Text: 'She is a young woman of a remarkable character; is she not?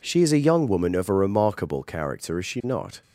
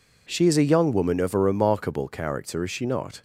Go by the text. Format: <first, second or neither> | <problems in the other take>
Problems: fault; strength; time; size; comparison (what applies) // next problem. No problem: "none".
neither | none